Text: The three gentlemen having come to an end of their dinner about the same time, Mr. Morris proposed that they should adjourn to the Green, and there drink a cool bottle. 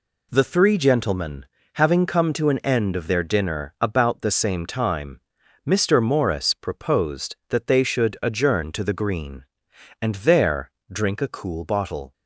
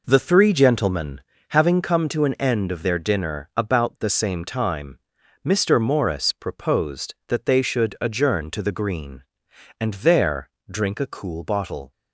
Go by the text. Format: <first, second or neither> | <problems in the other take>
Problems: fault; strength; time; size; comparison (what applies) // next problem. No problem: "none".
first | starts louder than the rest; noticeable; until 1.7 s; 4.5 dB // pauses between "gentlemen" and "having"; slight; at 1.2 s; 0.26 s long; slight in the first // pauses between "there" and "drink"; slight; at 10.4 s; 0.24 s long; slight in the first